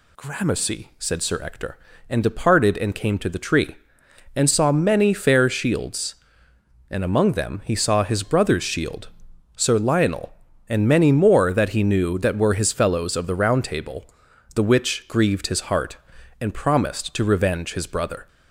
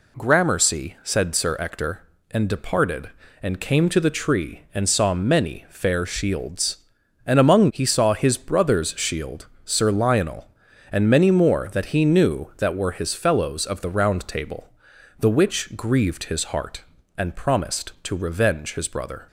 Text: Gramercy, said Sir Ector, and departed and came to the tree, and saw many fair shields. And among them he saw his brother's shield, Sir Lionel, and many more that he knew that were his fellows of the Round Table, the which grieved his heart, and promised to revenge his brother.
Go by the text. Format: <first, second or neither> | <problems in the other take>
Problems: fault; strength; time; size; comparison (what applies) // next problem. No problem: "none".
first | skips "them"; at 7.6 s